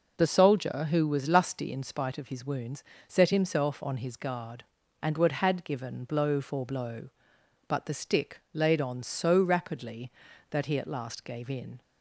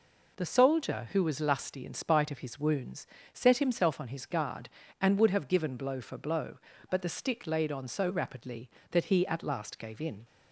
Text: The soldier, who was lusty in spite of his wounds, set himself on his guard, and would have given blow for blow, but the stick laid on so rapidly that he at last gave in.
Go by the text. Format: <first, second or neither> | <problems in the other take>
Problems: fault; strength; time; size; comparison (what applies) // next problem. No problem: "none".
second | says "had" for "have"; at 5.3 s